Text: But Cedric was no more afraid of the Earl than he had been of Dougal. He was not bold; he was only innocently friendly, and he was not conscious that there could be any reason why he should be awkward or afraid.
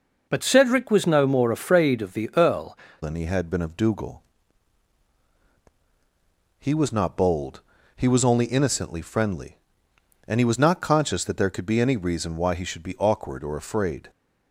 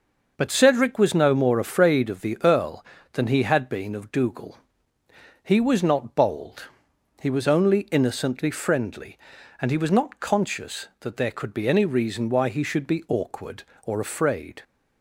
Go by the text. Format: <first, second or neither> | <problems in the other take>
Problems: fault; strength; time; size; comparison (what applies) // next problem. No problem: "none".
second | changes voice at "than"; from 3.0 s on; 11.0 s long